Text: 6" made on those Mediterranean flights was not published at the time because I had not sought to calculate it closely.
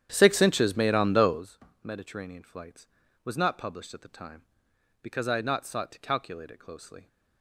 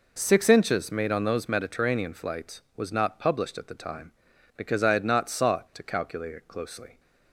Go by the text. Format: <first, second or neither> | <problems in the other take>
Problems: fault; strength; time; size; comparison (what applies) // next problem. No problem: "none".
second | starts louder than the rest; strong; until 1.5 s; 10 dB // pauses between "those" and "Mediterranean"; slight; at 1.5 s; 0.28 s long